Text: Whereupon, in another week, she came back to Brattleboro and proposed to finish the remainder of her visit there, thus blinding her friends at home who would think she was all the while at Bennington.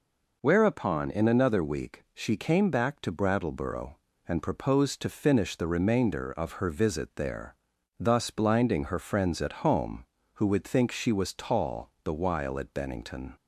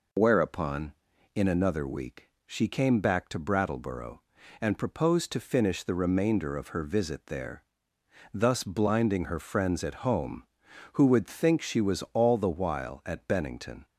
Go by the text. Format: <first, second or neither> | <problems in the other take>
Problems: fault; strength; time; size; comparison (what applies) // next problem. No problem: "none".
second | says "tall" for "all"; at 11.3 s